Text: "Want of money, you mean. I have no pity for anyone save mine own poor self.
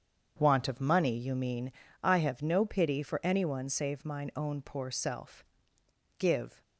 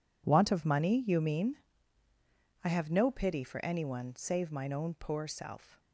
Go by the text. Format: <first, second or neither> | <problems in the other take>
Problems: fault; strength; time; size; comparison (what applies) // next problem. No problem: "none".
second | starts louder than the rest; strong; until 1.4 s; 7.5 dB // goes on to say "Give"; slight; from 6.1 s on; 0.42 s long